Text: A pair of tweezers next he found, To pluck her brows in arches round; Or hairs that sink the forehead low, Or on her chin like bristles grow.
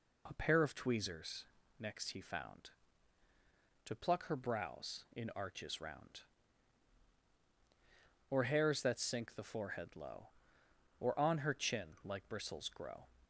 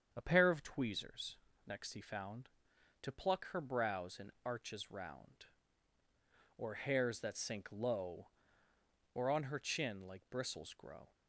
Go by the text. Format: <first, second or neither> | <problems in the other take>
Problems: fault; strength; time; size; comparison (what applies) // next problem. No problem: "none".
first | starts louder than the rest; strong; until 1.1 s; 7.5 dB // pauses between "tweezers" and "next"; slight; at 1.3 s; 0.28 s long; slight in the first // skips "the forehead"; at 7.7 s